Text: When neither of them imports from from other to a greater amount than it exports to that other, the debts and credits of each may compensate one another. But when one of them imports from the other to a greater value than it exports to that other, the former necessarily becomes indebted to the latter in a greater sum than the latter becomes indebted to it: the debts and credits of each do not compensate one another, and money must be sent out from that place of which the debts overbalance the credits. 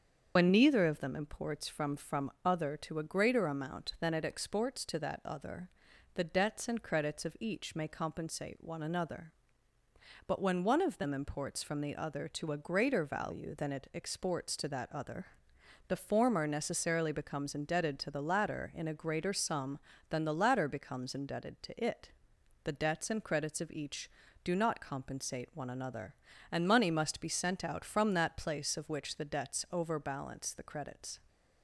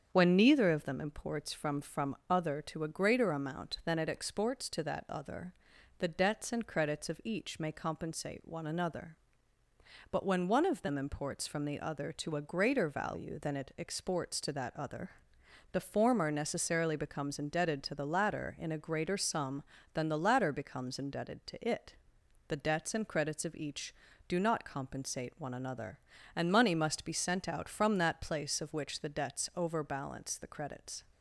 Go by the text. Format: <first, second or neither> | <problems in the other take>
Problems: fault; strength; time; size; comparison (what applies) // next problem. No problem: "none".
second | loses the start of "When"; at 0.3 s; 70 ms // starts louder than the rest; until 1.3 s; 7 dB; strong in the second